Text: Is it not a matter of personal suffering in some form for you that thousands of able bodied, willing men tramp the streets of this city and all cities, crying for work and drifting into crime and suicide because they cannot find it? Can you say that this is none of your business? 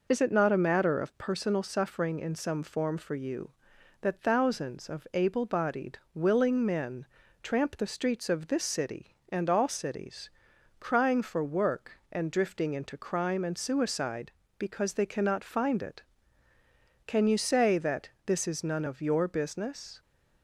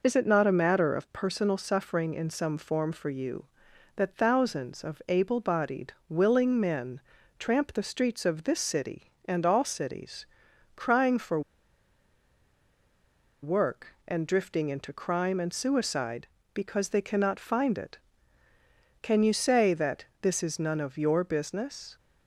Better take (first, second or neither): first